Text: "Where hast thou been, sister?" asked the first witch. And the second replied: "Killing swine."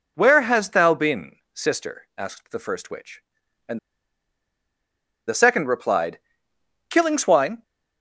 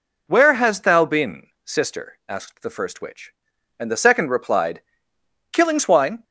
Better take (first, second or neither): second